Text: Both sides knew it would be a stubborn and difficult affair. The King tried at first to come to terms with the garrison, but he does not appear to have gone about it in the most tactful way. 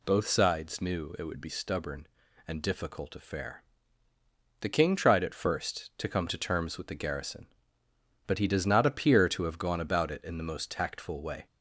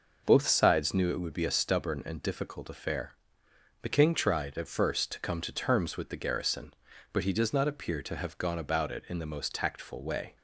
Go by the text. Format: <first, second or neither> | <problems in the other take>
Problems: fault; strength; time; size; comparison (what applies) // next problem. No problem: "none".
second | skips "a"; at 1.4 s